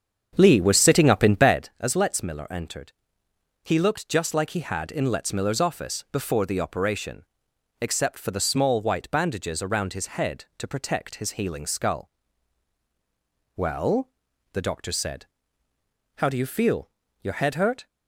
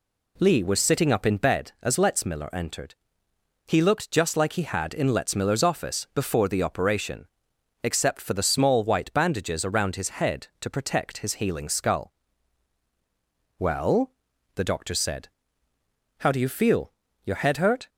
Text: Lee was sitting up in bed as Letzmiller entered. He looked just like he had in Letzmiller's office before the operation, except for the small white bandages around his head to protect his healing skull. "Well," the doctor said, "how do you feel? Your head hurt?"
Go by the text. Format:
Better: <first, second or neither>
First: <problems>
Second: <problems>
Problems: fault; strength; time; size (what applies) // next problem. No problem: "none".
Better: second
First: starts louder than the rest; strong; until 1.8 s; 7.5 dB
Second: none